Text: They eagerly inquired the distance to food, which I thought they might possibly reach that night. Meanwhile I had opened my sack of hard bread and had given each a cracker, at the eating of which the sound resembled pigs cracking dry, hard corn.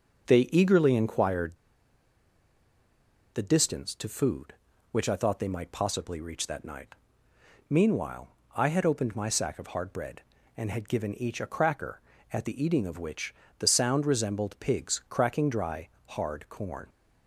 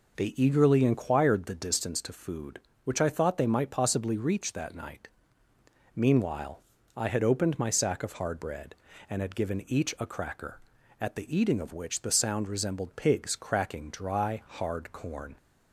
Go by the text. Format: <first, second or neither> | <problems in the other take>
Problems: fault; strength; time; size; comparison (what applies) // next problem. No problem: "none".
second | starts louder than the rest; until 1.3 s; 6.5 dB // pauses between "inquired" and "the"; strong; at 1.5 s; 1.7 s long // pauses between "Meanwhile" and "I"; slight; at 8.2 s; 0.28 s long; slight in the second // pauses between "which" and "the"; slight; at 13.3 s; 0.26 s long